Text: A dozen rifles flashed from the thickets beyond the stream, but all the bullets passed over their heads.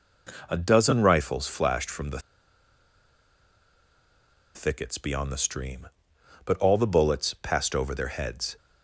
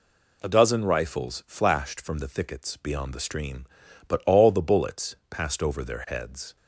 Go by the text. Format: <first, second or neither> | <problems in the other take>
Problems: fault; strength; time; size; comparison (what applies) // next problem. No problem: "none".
second | pauses between "the" and "thickets"; strong; at 2.1 s; 2.3 s long